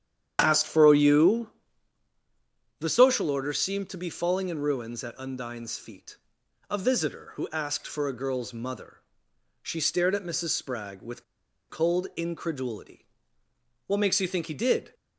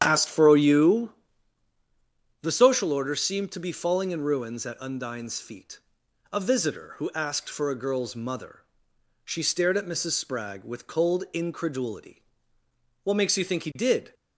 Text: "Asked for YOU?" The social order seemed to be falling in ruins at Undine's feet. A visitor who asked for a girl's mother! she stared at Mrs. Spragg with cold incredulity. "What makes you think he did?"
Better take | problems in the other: second | starts louder than the rest; strong; until 1.4 s; 9.5 dB; strong in the second // pauses between "with" and "cold"; noticeable; at 11.2 s; 0.47 s long

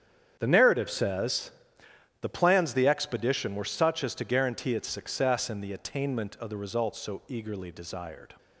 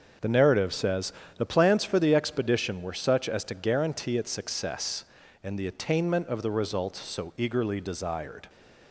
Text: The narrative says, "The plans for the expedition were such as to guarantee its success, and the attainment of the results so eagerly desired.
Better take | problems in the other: second | starts louder than the rest; strong; until 1.4 s; 8.5 dB; also in the second // skips "for"; at 2.7 s

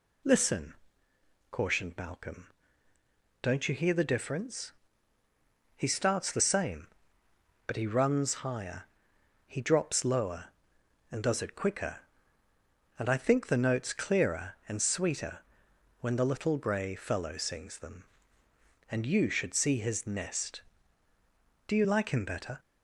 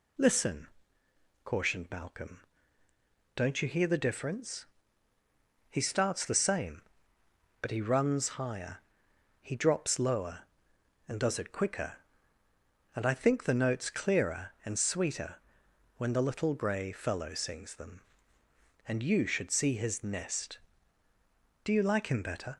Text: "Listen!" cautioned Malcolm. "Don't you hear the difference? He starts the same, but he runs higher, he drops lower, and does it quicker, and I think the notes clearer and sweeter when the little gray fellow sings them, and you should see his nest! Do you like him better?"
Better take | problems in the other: neither | pauses between "sweeter" and "when"; noticeable; the same in both

